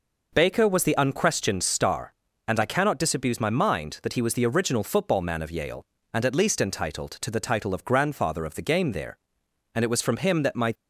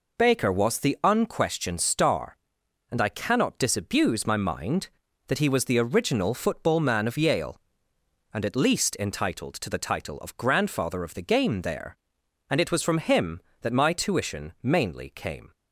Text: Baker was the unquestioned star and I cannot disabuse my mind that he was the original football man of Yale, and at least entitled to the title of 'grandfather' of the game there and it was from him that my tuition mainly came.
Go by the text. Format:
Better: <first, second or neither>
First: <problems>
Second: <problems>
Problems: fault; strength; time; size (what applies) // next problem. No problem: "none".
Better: second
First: stops before "tuition mainly came"; at 10.7 s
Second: none